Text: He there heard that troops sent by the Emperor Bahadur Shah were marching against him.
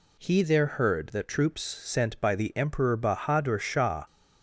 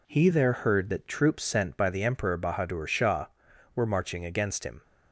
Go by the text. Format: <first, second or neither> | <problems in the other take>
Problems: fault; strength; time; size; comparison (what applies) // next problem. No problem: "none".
second | stops before "were marching against him"; at 4.0 s